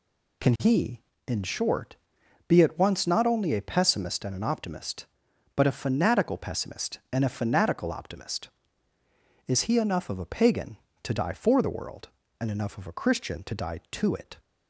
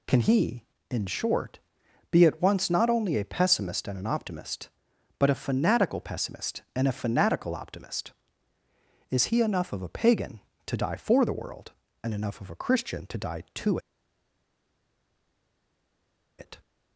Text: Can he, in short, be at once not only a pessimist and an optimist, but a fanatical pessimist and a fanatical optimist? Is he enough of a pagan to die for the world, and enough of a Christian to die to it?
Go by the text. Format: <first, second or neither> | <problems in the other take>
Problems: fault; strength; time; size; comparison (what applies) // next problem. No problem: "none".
first | pauses between "to" and "it"; strong; at 13.7 s; 2.6 s long